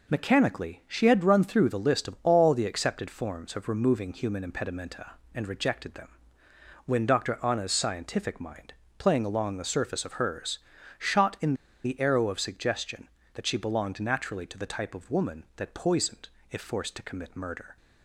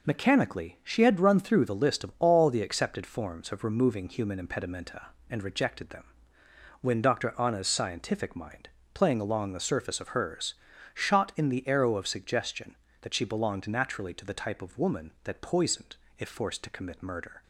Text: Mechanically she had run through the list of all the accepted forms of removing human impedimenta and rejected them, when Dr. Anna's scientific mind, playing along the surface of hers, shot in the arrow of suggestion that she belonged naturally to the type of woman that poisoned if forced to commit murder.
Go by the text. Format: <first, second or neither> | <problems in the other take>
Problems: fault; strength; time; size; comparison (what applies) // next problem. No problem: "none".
second | pauses between "in" and "the"; slight; at 11.5 s; 0.30 s long // pauses between "poisoned" and "if"; slight; at 16.2 s; 0.22 s long; slight in the second